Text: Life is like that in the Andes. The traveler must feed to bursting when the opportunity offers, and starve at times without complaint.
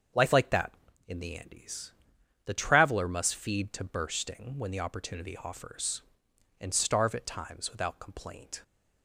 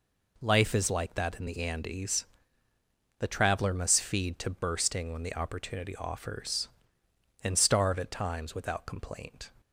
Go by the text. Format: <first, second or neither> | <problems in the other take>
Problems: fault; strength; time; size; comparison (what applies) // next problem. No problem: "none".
second | starts louder than the rest; until 1.4 s; 6.5 dB // skips "is"; at 0.3 s